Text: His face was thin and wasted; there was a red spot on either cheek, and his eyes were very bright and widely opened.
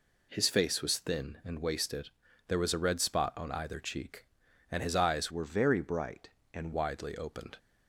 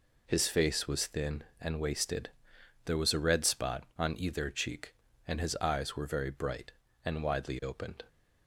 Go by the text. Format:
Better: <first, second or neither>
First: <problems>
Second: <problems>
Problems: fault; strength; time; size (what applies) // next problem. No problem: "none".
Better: second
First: changes voice from "were" to "and"; from 5.3 to 6.7 s; 1.4 s long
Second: none